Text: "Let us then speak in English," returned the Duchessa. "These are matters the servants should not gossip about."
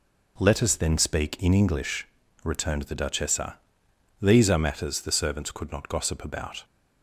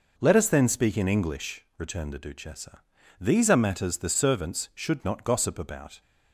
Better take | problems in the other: second | says "could" for "should"; at 5.5 s

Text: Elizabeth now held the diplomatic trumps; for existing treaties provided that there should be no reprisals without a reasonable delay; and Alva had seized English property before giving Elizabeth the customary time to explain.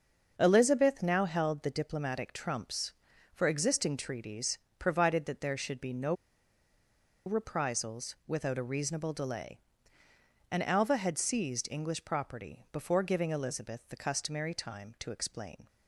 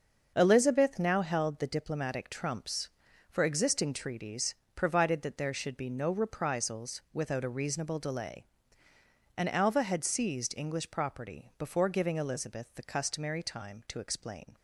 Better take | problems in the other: second | starts louder than the rest; until 1.4 s; 6.5 dB; also in the second // pauses between "treaties" and "provided"; slight; at 4.5 s; 0.22 s long; slight in the second // pauses between "no" and "reprisals"; at 6.1 s; 1.1 s long

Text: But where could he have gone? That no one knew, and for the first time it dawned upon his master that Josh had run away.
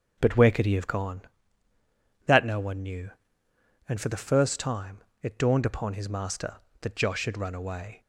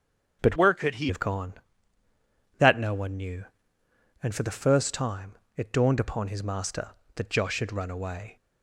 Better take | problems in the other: first | starts louder than the rest; until 1.4 s; 7 dB // changes voice from "where" to "he"; from 0.5 to 1.0 s; 0.5 s long // pauses between "time" and "it"; slight; at 5.3 s; 0.22 s long; slight in the first

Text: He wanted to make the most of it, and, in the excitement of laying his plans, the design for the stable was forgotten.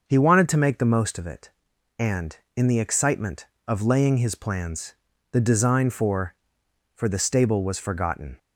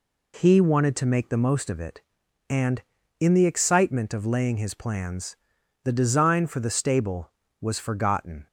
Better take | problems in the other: second | starts louder than the rest; until 1.1 s; 6 dB // says "for" twice; at 6.9 s

